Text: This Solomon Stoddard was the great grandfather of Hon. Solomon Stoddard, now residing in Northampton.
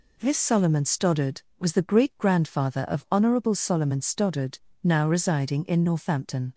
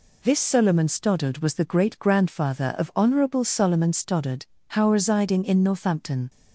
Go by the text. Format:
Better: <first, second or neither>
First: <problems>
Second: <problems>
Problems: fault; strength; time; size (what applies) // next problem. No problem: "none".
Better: first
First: none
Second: says "how" for "now"; at 4.6 s